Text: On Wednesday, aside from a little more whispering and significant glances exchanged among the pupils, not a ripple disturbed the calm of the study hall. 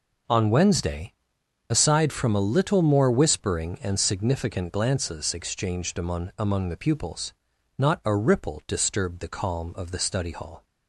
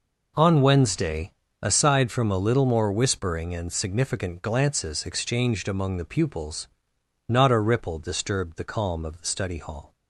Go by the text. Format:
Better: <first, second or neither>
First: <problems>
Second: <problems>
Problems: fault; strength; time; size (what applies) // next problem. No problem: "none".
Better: second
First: says "among" twice; at 6.3 s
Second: none